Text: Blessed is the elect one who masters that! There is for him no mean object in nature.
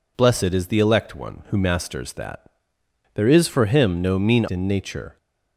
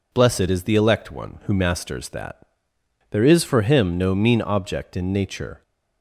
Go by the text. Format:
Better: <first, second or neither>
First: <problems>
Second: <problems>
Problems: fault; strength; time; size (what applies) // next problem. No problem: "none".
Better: second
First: skips "object"; at 4.4 s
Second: none